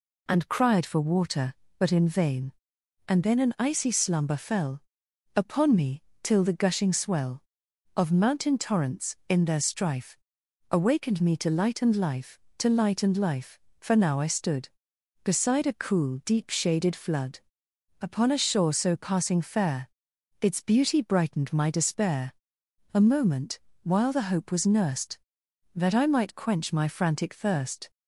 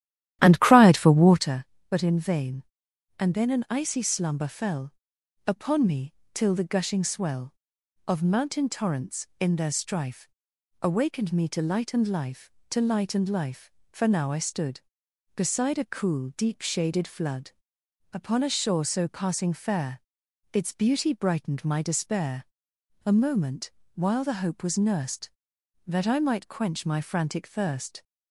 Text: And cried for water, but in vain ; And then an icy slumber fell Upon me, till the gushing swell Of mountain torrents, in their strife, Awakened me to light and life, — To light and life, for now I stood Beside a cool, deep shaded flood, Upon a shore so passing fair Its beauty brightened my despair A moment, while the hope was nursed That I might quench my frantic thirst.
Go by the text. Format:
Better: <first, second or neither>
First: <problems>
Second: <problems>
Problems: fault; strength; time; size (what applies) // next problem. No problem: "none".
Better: first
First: pauses between "fell" and "Upon"; noticeable; at 4.7 s; 0.56 s long // pauses between "fair" and "Its"; noticeable; at 19.8 s; 0.50 s long // pauses between "despair" and "A"; noticeable; at 22.3 s; 0.62 s long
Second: starts louder than the rest; strong; until 1.5 s; 12.5 dB // pauses between "fell" and "Upon"; noticeable; at 4.9 s; 0.56 s long // pauses between "fair" and "Its"; noticeable; at 20.0 s; 0.50 s long // pauses between "despair" and "A"; noticeable; at 22.4 s; 0.62 s long